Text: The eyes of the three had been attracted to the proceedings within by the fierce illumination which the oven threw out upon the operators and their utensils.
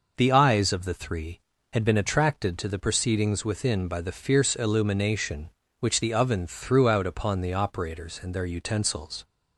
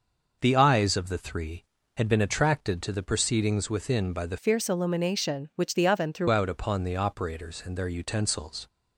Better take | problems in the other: first | changes voice from "fierce" to "threw"; from 4.3 to 6.2 s; 1.9 s long

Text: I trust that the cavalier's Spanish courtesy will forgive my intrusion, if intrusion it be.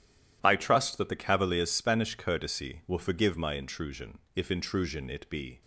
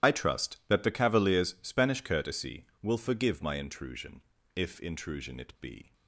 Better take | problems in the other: first | loses the start of "I"; at 0.0 s; 20 ms // starts louder than the rest; strong; until 1.1 s; 12 dB

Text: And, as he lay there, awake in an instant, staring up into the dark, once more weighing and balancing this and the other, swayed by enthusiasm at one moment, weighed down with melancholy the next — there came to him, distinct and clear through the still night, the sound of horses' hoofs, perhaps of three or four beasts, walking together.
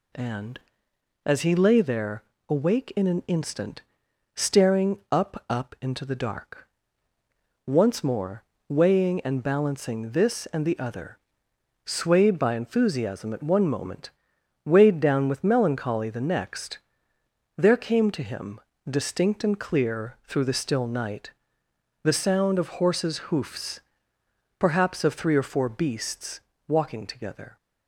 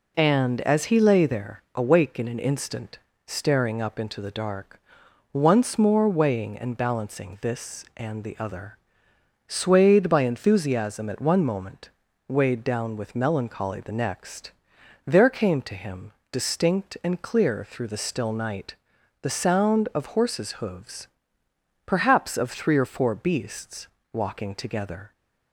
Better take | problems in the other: second | says "up" twice; at 5.4 s // pauses between "more" and "weighing"; slight; at 8.4 s; 0.26 s long

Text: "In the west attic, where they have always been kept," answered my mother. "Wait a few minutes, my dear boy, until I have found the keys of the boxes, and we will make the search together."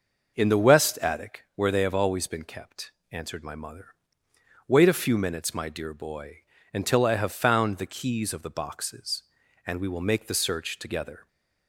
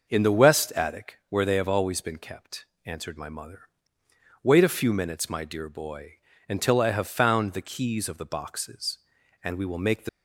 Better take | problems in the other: first | stops before "search together"; at 10.0 s

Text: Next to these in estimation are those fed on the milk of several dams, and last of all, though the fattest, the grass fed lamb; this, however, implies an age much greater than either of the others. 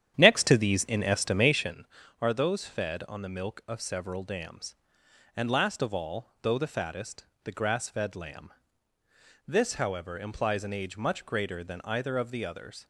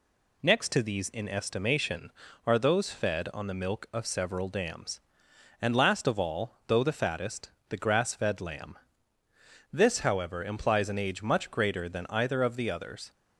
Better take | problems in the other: second | starts louder than the rest; strong; until 1.8 s; 10 dB

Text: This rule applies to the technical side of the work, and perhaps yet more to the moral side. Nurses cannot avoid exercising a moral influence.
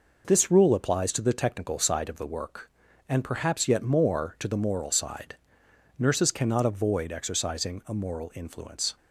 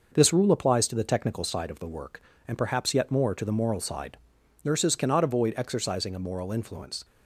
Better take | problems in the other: neither | none

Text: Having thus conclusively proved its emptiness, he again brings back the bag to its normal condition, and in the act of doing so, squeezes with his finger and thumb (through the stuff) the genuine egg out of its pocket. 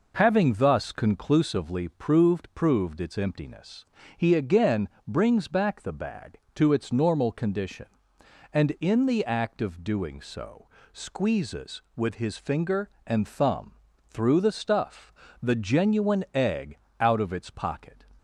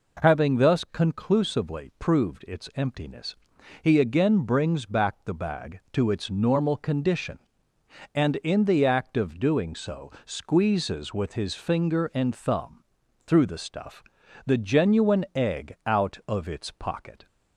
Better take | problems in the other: second | says "proved" twice; at 2.5 s // pauses between "again" and "brings"; slight; at 4.8 s; 0.18 s long // pauses between "egg" and "out"; slight; at 16.7 s; 0.20 s long

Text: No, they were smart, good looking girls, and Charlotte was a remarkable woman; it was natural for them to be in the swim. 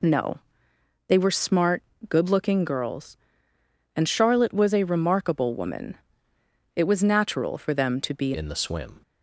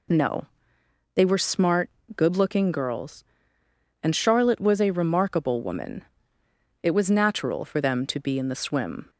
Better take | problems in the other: second | changes voice at "in"; from 8.3 s on; 0.7 s long

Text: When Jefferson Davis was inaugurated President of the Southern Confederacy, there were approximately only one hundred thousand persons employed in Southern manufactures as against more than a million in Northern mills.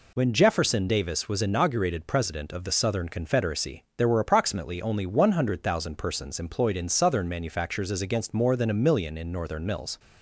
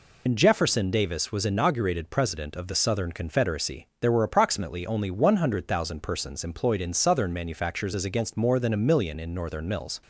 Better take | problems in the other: first | loses the start of "When"; at 0.2 s; 80 ms

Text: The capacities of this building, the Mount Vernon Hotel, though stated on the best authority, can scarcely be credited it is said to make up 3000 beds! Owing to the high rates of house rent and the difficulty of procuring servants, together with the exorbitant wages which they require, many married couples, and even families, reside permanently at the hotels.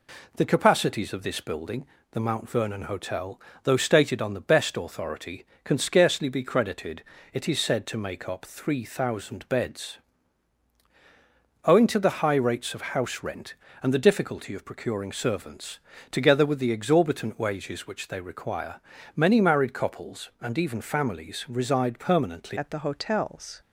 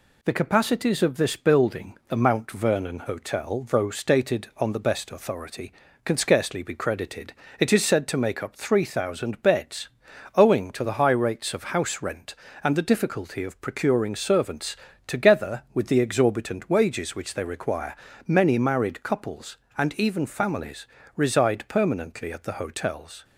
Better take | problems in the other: second | pauses between "credited" and "it"; slight; at 7.0 s; 0.30 s long; slight in the second // changes voice at "at"; from 22.5 s on; 1.1 s long

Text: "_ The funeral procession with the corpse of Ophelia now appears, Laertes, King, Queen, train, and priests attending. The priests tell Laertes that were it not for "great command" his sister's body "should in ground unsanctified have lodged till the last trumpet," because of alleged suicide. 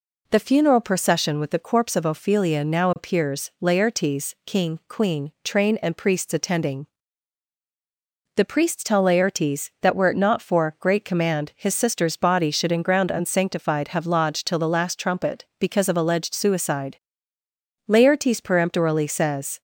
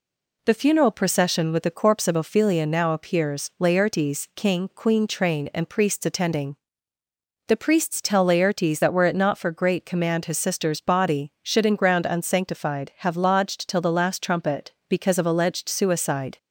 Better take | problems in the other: second | goes on to say "Laertes peremptorily says"; strong; from 17.8 s on; 1.7 s long

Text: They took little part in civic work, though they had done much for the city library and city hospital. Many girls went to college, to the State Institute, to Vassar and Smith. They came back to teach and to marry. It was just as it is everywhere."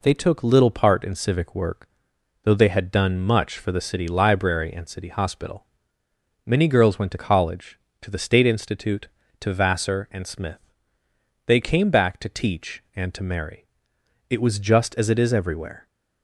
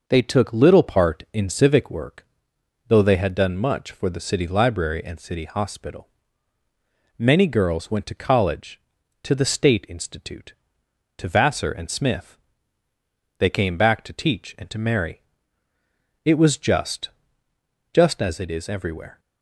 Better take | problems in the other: first | says "just" twice; at 17.9 s

